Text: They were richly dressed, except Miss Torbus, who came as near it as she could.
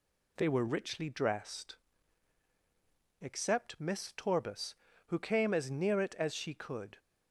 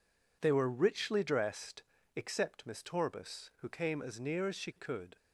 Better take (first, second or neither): first